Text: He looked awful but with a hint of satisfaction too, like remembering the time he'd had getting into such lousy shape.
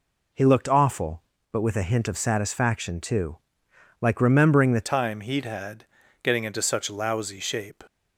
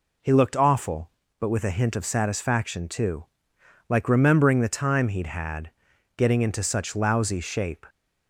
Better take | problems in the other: second | changes voice at "time"; from 4.8 s on; 3.0 s long // pauses between "had" and "getting"; slight; at 5.8 s; 0.36 s long; noticeable in the second

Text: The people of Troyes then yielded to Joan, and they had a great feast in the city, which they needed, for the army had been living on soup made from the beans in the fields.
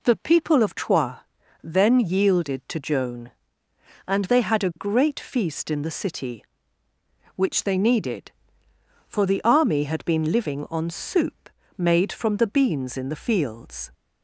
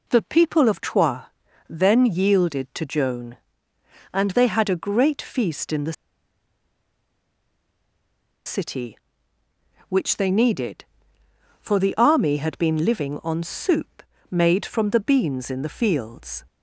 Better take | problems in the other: first | pauses between "Troyes" and "then"; at 1.2 s; 0.44 s long; also in the first // pauses between "the" and "city"; strong; at 5.9 s; 2.5 s long // pauses between "soup" and "made"; slight; at 14.0 s; 0.28 s long; slight in the first

